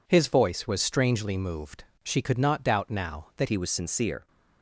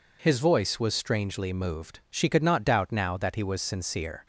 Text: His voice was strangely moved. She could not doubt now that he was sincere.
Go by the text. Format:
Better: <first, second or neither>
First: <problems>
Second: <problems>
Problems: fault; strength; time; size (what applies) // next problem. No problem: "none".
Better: second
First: changes voice at "he"; from 3.4 s on; 0.8 s long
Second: none